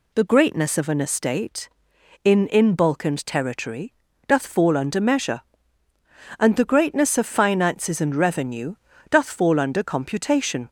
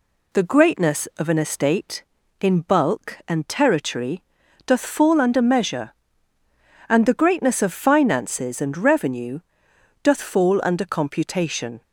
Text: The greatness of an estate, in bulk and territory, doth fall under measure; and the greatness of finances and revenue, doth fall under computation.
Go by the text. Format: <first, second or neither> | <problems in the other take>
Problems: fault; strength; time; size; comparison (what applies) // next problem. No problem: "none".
second | says "in" twice; at 2.4 s